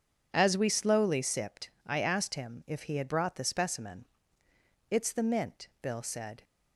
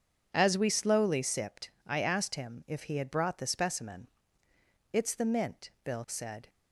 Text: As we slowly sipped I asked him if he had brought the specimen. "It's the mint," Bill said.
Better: neither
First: pauses between "sipped" and "I"; slight; at 1.6 s; 0.18 s long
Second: pauses between "sipped" and "I"; slight; at 1.6 s; 0.18 s long

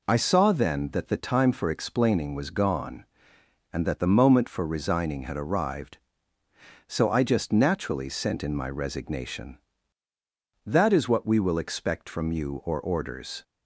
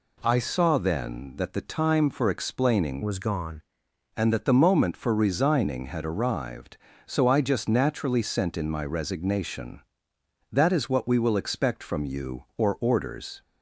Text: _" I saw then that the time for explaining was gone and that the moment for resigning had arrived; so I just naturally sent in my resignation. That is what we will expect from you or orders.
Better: first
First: none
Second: changes voice from "was" to "gone"; from 3.0 to 3.6 s; 0.6 s long

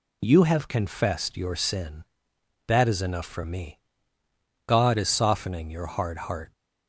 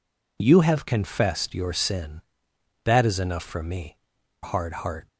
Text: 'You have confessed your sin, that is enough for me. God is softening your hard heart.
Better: first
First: none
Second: skips "God is softening your"; at 4.1 s

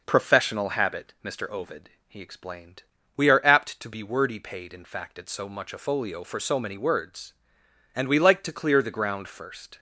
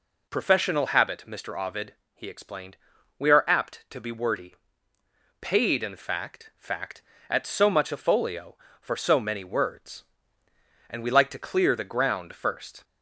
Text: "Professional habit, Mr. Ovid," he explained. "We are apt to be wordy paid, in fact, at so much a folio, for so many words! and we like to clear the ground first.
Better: first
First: none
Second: pauses between "wordy" and "paid"; noticeable; at 4.5 s; 0.84 s long // says "fact" twice; at 6.5 s

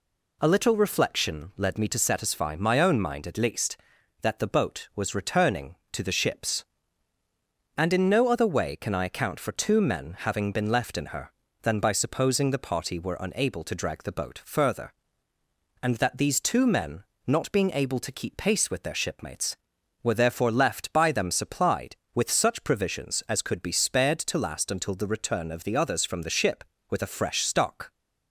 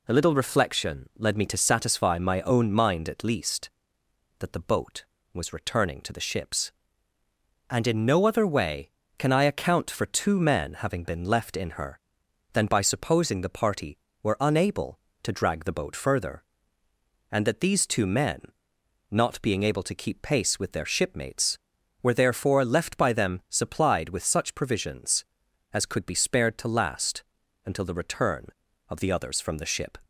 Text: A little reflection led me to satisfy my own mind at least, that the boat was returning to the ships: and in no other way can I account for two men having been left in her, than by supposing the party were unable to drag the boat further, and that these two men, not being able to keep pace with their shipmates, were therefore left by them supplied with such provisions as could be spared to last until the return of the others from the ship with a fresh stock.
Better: first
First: none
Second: pauses between "last" and "until"; at 27.2 s; 0.42 s long // stops before "with a fresh stock"; at 30.0 s

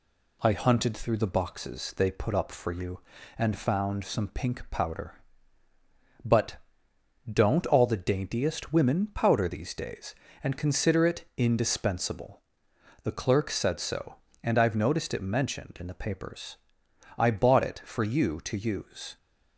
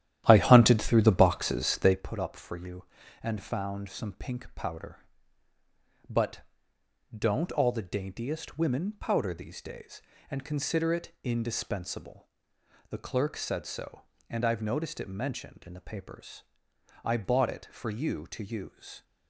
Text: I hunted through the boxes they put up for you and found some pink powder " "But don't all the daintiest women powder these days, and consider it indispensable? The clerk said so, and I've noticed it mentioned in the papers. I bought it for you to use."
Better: first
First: pauses between "But" and "don't"; noticeable; at 6.5 s; 0.73 s long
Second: starts louder than the rest; strong; until 2.1 s; 12.5 dB // pauses between "But" and "don't"; noticeable; at 6.3 s; 0.74 s long

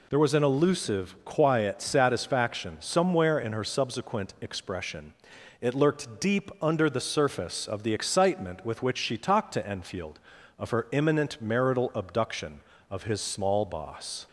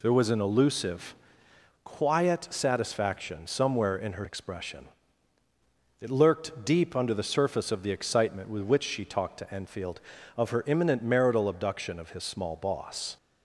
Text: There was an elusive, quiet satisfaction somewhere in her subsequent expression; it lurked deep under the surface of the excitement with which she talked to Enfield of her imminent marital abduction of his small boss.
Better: first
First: none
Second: skips "subsequent"; at 4.2 s

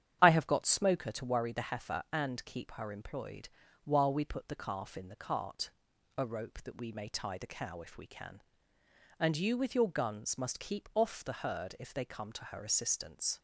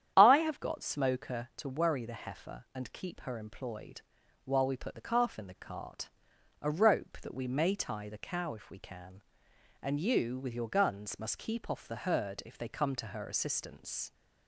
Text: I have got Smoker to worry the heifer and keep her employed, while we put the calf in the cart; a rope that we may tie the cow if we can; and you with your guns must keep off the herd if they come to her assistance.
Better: neither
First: starts louder than the rest; strong; until 1.2 s; 9.5 dB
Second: starts louder than the rest; strong; until 1.1 s; 10 dB

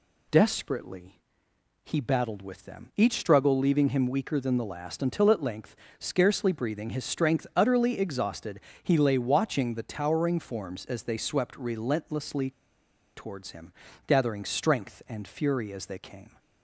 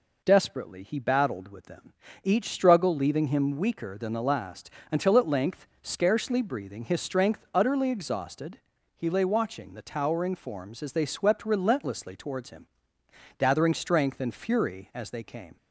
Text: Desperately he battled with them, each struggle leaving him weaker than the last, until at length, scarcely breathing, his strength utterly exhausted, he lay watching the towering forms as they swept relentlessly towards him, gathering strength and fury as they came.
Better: second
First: pauses between "Desperately" and "he"; noticeable; at 1.1 s; 0.72 s long // pauses between "relentlessly" and "towards"; noticeable; at 12.5 s; 0.64 s long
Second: none

